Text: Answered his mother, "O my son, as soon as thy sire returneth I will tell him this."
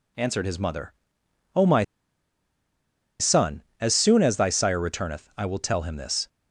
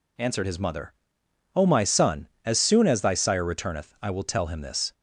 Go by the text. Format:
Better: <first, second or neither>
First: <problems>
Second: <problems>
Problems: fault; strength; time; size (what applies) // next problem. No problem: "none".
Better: second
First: pauses between "my" and "son"; strong; at 1.8 s; 1.3 s long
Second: none